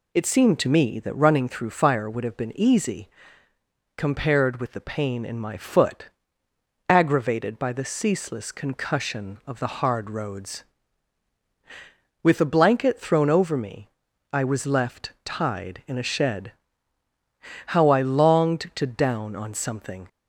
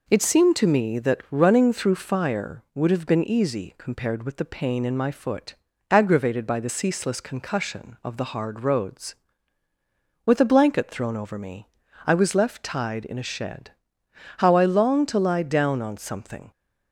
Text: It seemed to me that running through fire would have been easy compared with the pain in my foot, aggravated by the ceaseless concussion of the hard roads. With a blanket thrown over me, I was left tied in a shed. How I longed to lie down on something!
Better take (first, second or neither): second